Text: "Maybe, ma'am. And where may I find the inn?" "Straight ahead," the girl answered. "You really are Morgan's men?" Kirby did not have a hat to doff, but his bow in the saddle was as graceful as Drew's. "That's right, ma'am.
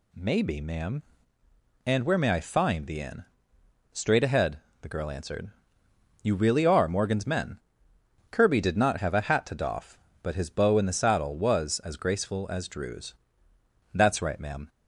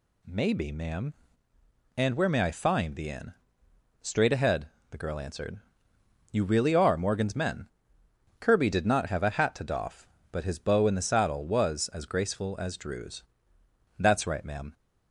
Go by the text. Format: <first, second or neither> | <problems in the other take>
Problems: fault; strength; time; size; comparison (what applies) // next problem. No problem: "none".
neither | none